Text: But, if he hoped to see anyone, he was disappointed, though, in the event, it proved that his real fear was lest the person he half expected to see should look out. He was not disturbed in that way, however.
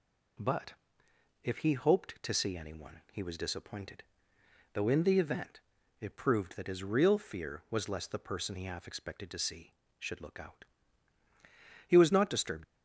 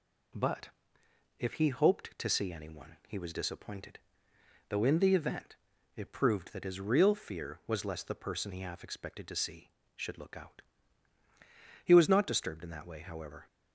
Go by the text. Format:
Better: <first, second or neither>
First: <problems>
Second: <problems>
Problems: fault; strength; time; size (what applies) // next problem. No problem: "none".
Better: second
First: stops before "in that way however"; at 12.6 s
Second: none